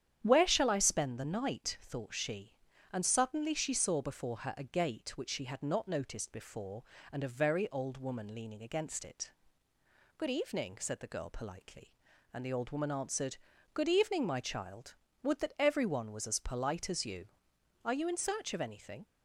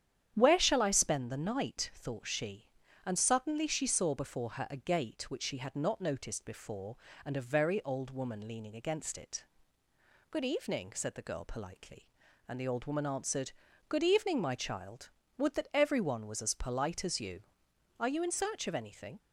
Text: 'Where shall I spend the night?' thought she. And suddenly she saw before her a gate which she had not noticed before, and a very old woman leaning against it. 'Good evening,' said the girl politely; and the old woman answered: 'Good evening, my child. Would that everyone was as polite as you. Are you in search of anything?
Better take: neither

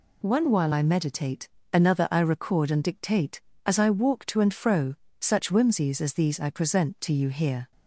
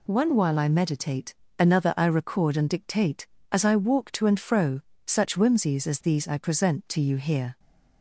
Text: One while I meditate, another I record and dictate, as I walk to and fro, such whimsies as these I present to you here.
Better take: neither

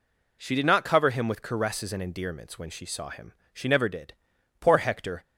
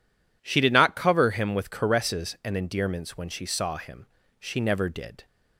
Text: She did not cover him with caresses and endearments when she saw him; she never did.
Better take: second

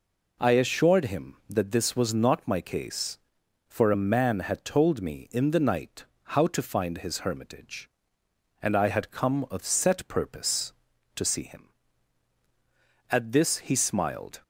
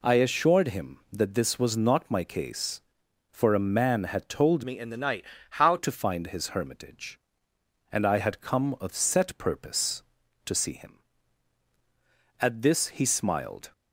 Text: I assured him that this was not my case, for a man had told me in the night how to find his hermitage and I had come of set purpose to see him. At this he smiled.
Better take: first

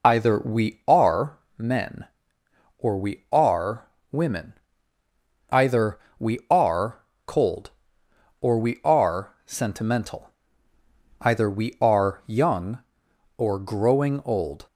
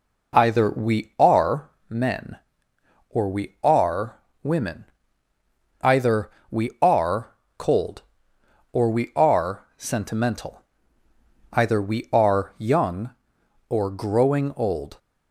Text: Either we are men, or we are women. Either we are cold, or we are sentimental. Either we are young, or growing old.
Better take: second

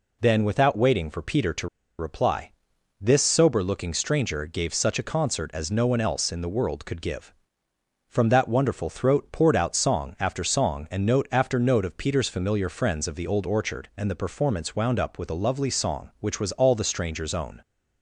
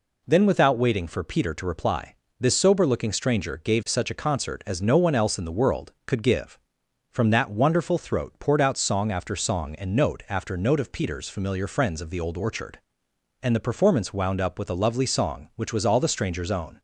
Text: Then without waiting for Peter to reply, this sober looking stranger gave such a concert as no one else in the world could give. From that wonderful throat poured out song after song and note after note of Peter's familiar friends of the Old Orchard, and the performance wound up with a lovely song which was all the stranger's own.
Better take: second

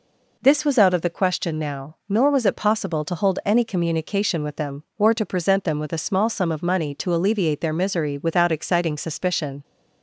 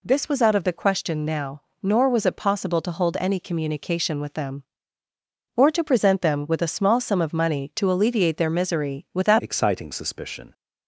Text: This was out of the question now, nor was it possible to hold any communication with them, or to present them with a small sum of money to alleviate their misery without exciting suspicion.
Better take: first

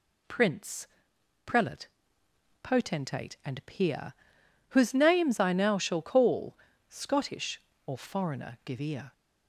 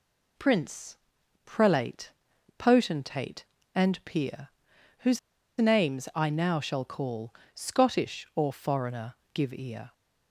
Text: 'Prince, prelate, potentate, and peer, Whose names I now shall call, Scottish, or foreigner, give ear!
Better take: first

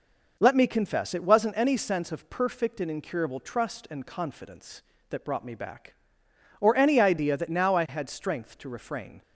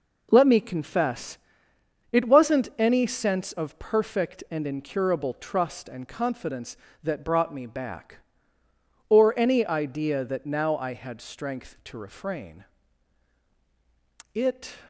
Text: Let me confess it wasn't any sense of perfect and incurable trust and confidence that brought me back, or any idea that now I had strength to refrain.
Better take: first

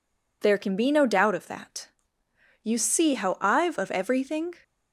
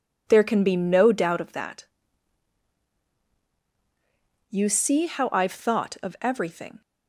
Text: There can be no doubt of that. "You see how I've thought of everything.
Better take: second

